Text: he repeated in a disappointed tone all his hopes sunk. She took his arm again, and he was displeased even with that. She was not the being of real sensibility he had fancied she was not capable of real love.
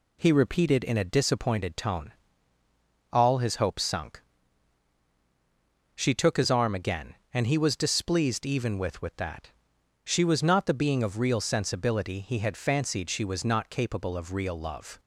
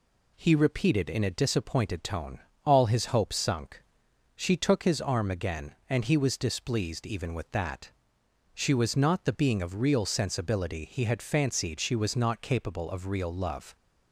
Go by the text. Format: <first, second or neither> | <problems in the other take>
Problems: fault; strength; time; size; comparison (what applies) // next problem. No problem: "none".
second | pauses between "tone" and "all"; at 2.1 s; 1.0 s long; slight in the second // says "with" twice; at 9.0 s